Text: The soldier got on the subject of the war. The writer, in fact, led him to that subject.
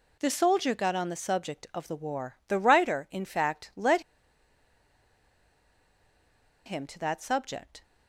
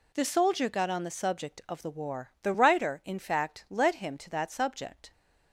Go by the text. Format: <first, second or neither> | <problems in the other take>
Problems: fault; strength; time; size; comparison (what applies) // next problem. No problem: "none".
second | pauses between "led" and "him"; strong; at 4.0 s; 2.6 s long